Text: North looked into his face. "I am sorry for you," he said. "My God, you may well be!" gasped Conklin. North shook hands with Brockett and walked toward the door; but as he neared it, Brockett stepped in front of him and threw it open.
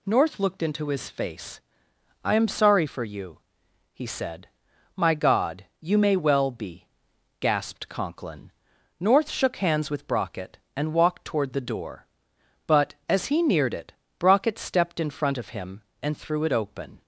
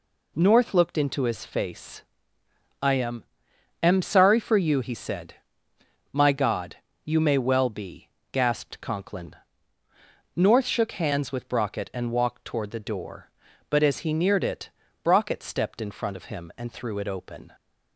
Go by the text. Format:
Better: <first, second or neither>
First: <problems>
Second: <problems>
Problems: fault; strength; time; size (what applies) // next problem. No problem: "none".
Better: first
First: none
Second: says "am" twice; at 3.8 s